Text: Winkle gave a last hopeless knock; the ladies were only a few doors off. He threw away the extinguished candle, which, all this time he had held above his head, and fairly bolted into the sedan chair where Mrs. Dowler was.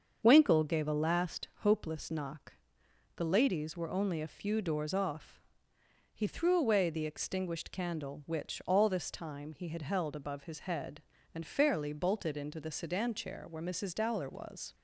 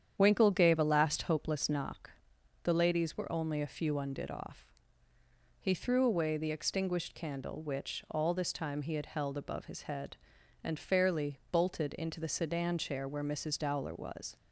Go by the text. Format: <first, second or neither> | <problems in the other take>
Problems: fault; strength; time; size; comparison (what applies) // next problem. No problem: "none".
first | starts louder than the rest; strong; until 1.1 s; 9 dB; also in the first // says "undid" for "doors"; at 3.9 s